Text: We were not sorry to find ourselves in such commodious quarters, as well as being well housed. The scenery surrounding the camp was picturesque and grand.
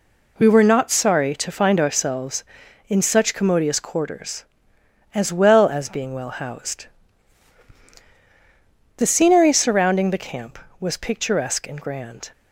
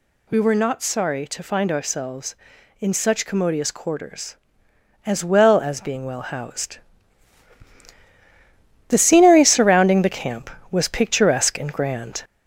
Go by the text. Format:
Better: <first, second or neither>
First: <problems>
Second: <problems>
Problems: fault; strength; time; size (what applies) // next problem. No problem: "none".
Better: first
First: none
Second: gets louder; slight; throughout; 3 dB